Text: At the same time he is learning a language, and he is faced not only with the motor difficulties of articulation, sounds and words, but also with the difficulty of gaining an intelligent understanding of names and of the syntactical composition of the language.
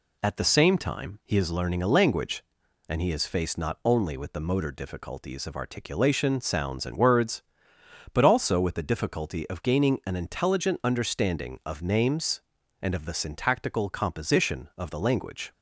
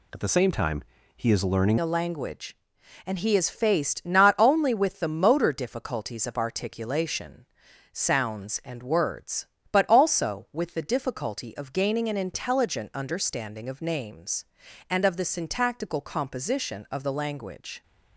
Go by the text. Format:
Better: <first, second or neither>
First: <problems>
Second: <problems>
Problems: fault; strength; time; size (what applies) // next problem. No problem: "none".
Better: first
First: none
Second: pauses between "time" and "he"; slight; at 0.8 s; 0.34 s long // changes voice at "a"; from 1.8 s on; 16.0 s long